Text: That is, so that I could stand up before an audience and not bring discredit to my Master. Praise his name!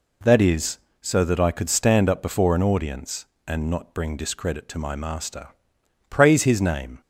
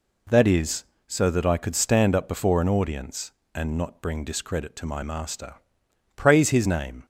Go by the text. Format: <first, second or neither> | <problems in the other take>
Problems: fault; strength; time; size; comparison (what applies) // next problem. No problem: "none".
neither | none